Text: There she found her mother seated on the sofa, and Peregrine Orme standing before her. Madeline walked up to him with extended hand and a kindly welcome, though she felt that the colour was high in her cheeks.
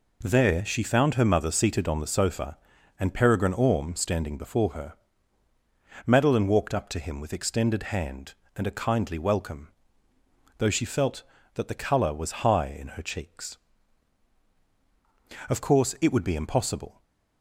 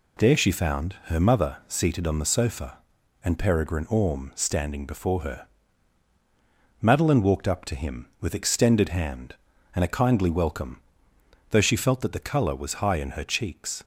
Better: second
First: goes on to say "Of course it would be impossible"; from 15.4 s on; 1.5 s long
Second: none

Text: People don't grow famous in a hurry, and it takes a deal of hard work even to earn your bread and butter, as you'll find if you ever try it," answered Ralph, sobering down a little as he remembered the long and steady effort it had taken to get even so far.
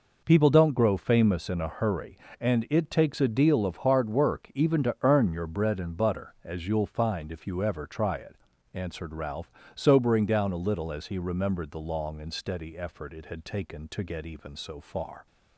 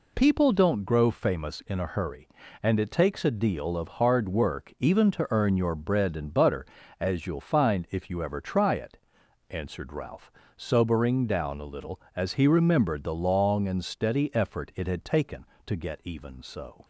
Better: first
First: none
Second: stops before "far"; at 16.8 s

